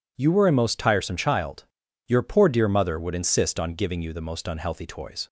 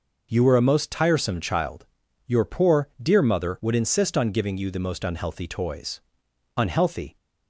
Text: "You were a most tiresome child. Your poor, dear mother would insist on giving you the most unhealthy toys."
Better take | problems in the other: first | goes on to say "Unhealthy"; from 6.5 s on; 0.60 s long

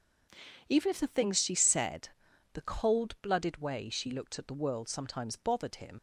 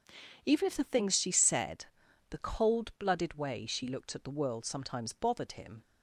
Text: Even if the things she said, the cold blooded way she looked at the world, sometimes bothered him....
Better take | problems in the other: second | leaves "him" unfinished; at 5.9 s; 60 ms

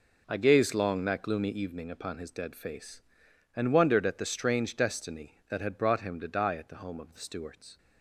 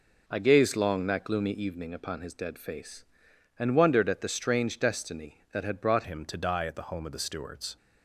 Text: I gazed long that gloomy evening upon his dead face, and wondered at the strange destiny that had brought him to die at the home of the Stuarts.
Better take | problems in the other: first | changes voice at "him"; from 6.0 s on; 1.7 s long

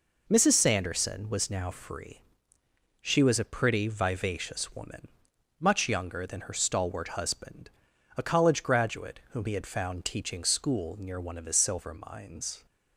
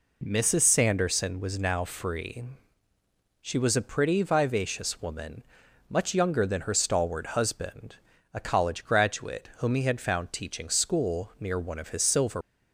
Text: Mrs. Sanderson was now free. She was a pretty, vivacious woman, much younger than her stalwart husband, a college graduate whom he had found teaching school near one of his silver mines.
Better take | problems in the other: first | stops before "mines"; at 12.4 s

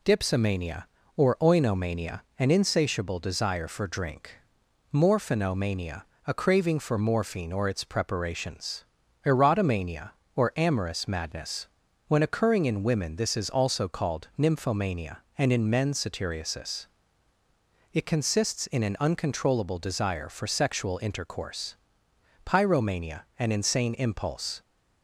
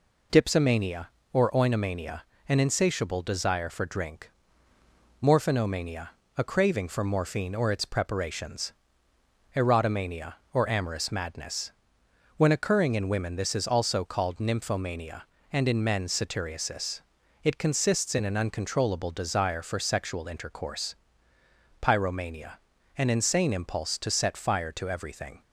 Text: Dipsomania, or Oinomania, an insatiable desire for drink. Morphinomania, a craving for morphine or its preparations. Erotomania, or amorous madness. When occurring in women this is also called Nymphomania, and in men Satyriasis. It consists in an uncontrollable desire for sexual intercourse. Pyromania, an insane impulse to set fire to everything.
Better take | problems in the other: second | stops before "to set fire to everything"; at 24.6 s

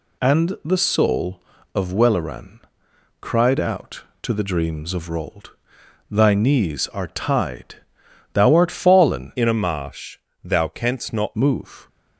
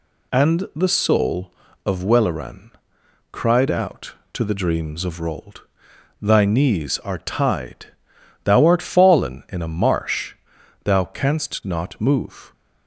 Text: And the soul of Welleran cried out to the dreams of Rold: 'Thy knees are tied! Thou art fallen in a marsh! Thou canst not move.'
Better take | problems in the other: second | pauses between "Welleran" and "cried"; noticeable; at 2.6 s; 0.60 s long; noticeable in the second // changes voice from "in" to "not"; from 9.3 to 11.3 s; 2.0 s long

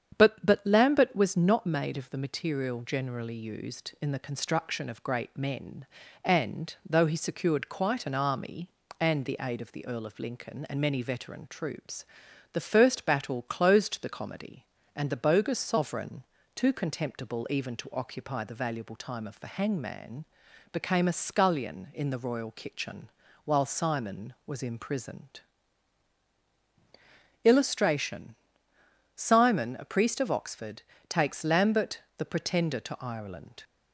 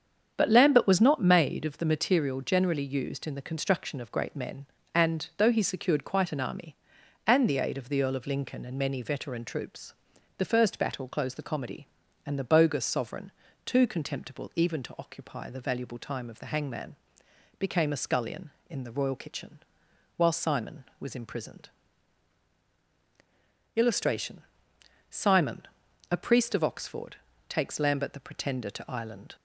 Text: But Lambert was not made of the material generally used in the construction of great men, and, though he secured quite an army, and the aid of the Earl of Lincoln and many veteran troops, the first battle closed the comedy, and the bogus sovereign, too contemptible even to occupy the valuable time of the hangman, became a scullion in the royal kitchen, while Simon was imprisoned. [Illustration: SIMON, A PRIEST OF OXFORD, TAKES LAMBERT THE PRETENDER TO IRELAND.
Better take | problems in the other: second | starts louder than the rest; strong; until 1.2 s; 8 dB; strong in the second // says "But" twice; at 0.4 s // pauses between "LAMBERT" and "THE"; slight; at 32.0 s; 0.16 s long

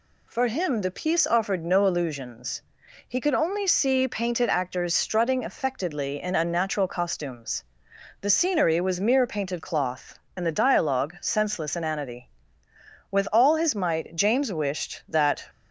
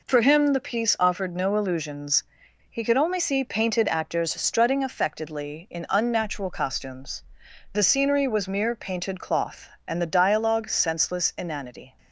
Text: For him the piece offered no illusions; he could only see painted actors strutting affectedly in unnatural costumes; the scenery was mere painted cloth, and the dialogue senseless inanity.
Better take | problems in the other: second | goes on to say "With all his might James wished that"; strong; from 13.0 s on; 2.3 s long

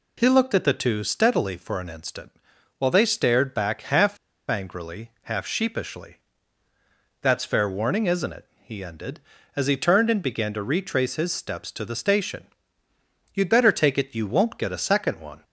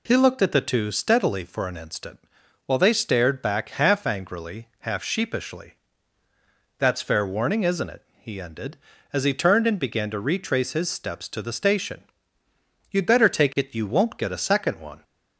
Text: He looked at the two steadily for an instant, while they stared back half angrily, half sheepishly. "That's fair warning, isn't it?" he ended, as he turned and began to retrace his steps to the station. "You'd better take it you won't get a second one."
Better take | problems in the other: second | pauses between "half" and "angrily"; slight; at 4.1 s; 0.31 s long

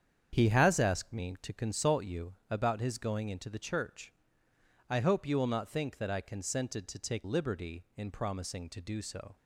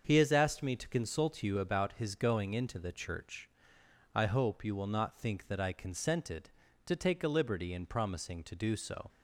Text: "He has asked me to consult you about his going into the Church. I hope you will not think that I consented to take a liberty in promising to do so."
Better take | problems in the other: second | starts louder than the rest; strong; until 1.3 s; 8 dB; also in the second // pauses between "you" and "about"; slight; at 2.3 s; 0.16 s long // skips "a"; at 7.2 s

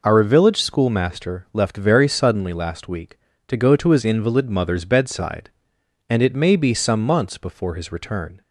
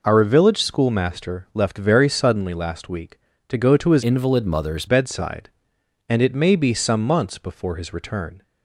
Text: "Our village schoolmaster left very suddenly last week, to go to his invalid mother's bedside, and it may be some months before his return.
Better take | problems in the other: first | changes voice from "invalid" to "mother's"; from 4.0 to 4.8 s; 0.8 s long

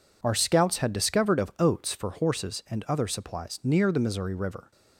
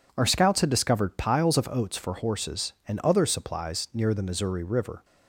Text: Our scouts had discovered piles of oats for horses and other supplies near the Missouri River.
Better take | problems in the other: second | skips "piles"; at 1.3 s

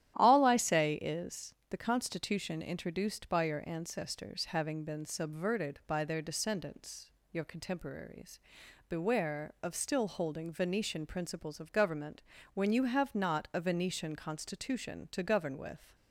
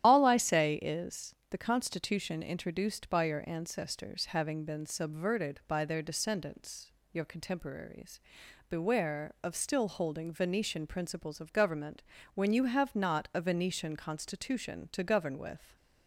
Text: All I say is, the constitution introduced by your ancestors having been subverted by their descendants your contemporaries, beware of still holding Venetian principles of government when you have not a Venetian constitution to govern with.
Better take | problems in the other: first | loses the start of "All"; at 0.0 s; 95 ms // starts louder than the rest; strong; until 1.1 s; 11.5 dB; strong in the first // pauses between "descendants" and "your"; slight; at 6.9 s; 0.22 s long; slight in the first // pauses between "government" and "when"; slight; at 12.0 s; 0.30 s long; slight in the first

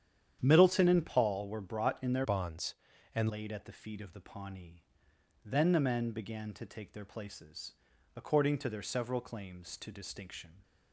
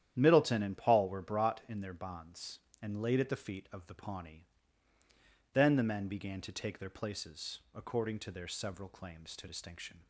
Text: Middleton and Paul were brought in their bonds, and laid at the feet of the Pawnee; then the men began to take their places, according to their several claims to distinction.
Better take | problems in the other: second | starts louder than the rest; strong; until 1.4 s; 9.5 dB; strong in the second // changes voice from "bonds" to "and"; from 2.2 to 3.3 s; 1.1 s long

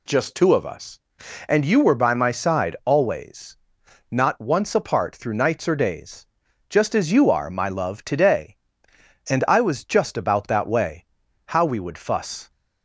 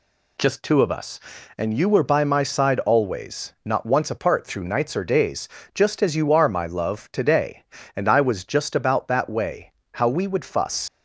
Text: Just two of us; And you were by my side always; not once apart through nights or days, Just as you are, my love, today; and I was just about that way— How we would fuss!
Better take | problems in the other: first | leaves "fuss" unfinished; at 10.8 s; 70 ms

